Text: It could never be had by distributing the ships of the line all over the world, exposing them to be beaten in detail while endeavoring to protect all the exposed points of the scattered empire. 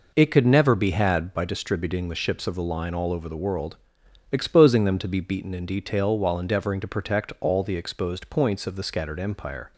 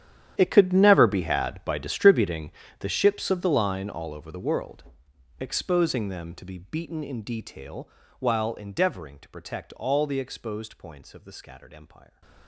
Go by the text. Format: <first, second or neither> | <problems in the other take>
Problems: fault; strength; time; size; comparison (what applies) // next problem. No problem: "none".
first | gets quieter; strong; throughout; 19.5 dB // pauses between "distributing" and "the"; slight; at 2.5 s; 0.28 s long // pauses between "detail" and "while"; slight; at 7.8 s; 0.30 s long